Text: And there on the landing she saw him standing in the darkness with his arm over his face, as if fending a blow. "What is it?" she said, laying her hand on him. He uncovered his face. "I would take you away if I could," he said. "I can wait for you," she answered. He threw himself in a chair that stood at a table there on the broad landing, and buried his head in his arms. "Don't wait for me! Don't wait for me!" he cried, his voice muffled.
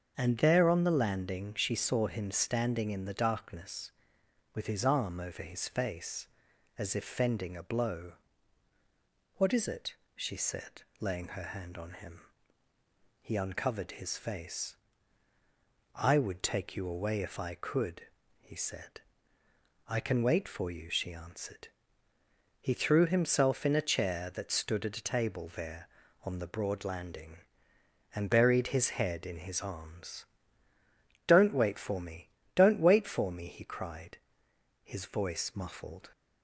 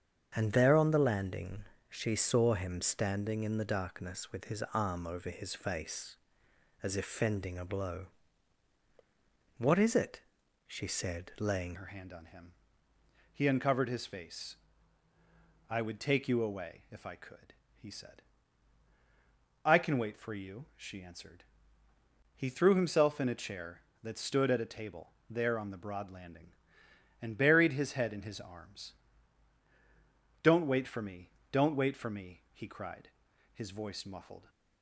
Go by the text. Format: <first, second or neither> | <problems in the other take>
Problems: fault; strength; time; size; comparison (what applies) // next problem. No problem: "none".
first | starts louder than the rest; strong; until 1.3 s; 7.5 dB; also in the first // pauses between "landing" and "she"; slight; at 1.6 s; 0.26 s long // changes voice at "her"; from 11.7 s on; 22.7 s long